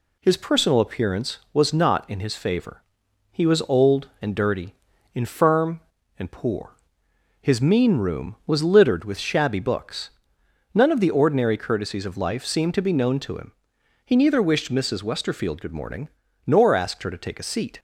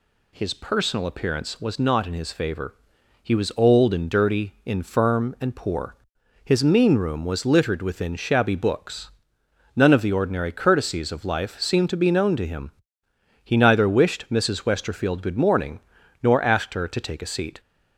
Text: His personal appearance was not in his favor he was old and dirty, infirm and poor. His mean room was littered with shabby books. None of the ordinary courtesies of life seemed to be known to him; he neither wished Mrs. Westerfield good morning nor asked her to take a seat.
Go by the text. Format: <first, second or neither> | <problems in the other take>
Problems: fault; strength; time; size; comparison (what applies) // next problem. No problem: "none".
first | pauses between "favor" and "he"; noticeable; at 2.7 s; 0.52 s long; noticeable in the first // says "within" for "with"; at 7.7 s // pauses between "morning" and "nor"; at 15.7 s; 0.42 s long; also in the first